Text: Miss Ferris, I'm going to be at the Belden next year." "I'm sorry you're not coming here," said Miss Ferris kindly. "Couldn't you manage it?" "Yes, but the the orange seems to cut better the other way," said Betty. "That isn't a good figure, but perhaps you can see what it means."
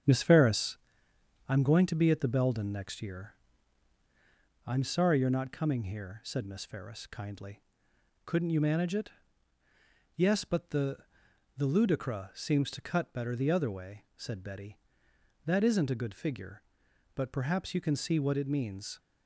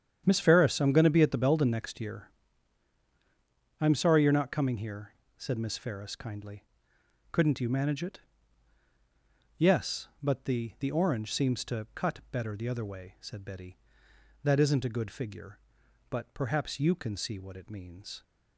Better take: second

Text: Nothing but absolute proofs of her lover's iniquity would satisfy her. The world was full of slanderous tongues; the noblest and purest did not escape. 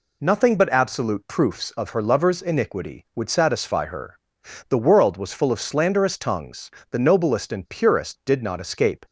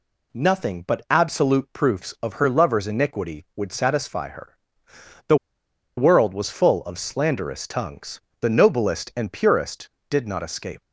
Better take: first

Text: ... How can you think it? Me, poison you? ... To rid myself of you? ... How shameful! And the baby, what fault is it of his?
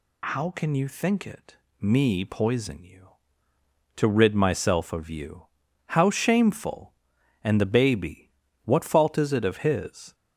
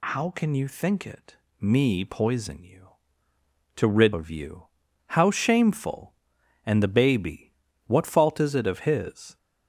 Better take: first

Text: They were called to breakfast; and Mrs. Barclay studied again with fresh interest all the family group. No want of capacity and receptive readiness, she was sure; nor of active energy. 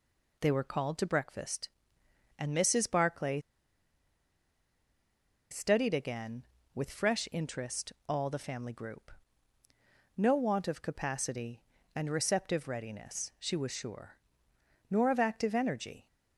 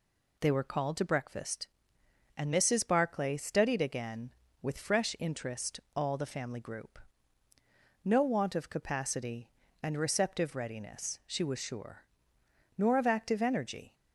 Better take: second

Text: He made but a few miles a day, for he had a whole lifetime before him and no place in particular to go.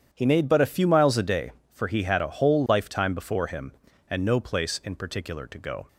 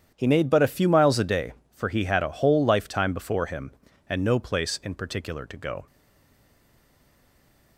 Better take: first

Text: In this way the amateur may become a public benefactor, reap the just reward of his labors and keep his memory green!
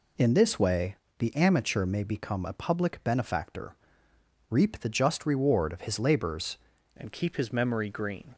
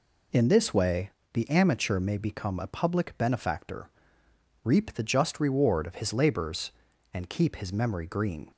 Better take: second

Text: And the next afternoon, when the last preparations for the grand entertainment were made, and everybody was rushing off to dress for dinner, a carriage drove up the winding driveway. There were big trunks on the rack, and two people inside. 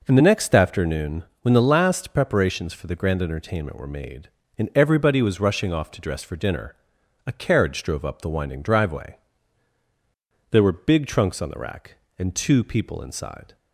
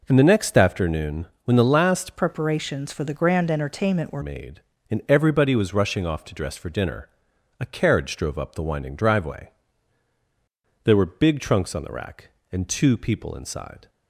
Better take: first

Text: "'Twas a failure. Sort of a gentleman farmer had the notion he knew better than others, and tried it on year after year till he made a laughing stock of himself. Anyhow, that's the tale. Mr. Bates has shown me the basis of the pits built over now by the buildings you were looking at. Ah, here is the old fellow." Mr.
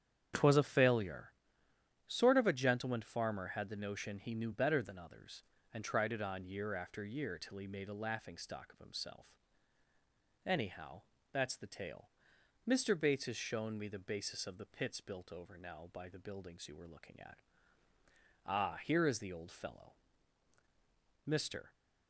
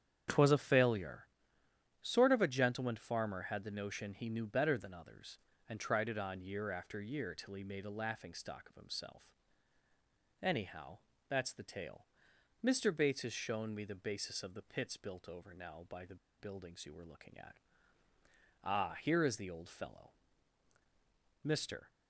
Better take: first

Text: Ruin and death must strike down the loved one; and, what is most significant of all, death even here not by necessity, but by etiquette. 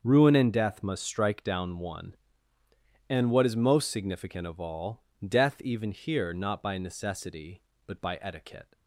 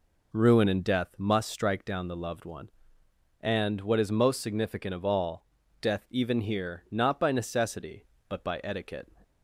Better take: second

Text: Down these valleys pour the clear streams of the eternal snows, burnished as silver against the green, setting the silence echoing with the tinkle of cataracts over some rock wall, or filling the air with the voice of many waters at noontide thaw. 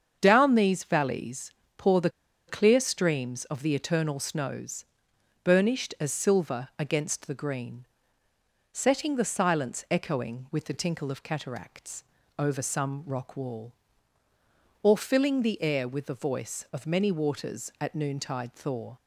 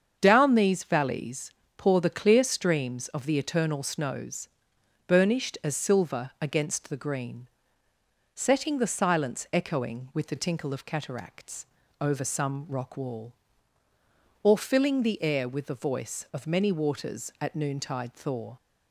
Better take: second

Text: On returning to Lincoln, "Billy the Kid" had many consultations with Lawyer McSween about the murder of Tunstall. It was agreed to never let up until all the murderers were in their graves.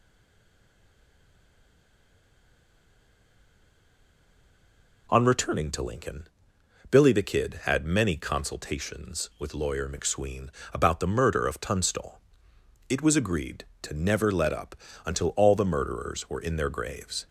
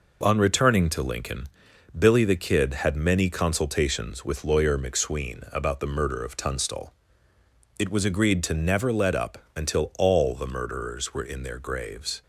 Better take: second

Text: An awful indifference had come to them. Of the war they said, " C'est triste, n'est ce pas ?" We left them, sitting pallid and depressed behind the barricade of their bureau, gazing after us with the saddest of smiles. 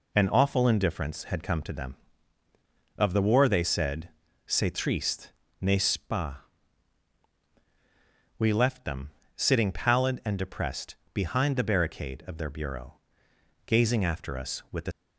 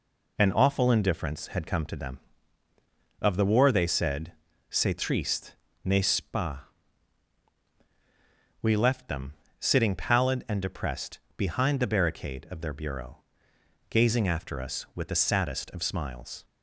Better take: second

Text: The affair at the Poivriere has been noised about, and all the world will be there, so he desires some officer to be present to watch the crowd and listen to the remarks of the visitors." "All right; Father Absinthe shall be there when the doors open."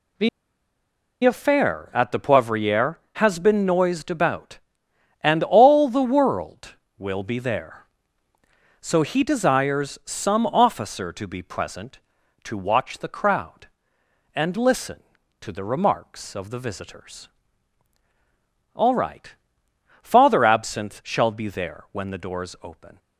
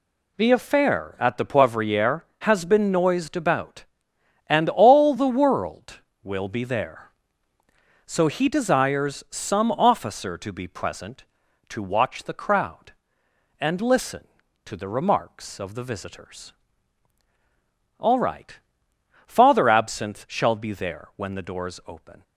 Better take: second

